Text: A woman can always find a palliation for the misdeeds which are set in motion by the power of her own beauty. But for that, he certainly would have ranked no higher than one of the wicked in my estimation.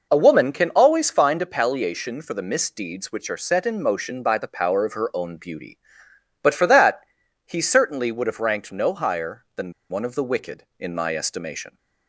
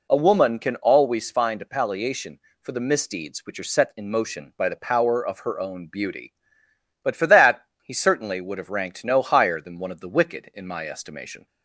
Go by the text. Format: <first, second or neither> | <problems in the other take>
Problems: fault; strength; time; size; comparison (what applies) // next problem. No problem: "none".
second | pauses between "than" and "one"; slight; at 9.7 s; 0.18 s long